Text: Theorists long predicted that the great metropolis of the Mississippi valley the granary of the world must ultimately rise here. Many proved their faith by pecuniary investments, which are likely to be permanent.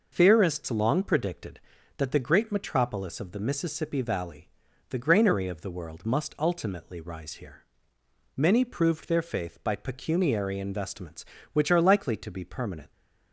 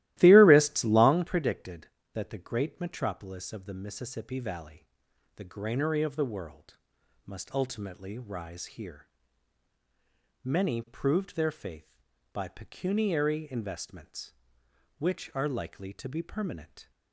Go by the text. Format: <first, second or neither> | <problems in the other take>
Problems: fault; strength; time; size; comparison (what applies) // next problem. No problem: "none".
first | starts louder than the rest; strong; until 1.3 s; 16 dB // pauses between "valley" and "the"; noticeable; at 4.8 s; 0.48 s long; also in the first // pauses between "world" and "must"; noticeable; at 6.7 s; 0.50 s long